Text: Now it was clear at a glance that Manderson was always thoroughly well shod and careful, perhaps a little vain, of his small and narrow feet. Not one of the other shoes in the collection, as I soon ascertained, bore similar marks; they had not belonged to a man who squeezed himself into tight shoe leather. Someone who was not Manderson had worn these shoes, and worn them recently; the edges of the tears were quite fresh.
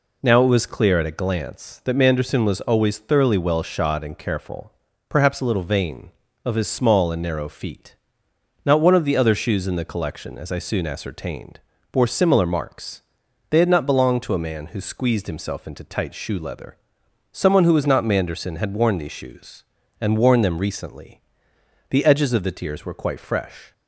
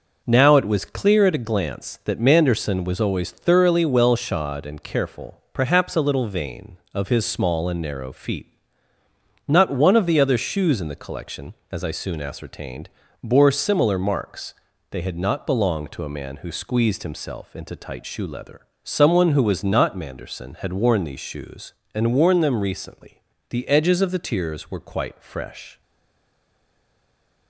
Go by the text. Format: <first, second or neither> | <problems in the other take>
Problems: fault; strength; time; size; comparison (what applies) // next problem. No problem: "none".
first | stays silent after the last word; noticeable; from 25.8 s on; 1.6 s long